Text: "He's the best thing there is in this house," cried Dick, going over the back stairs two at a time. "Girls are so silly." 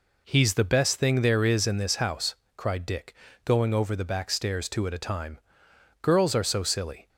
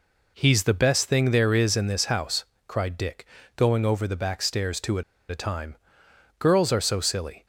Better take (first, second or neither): first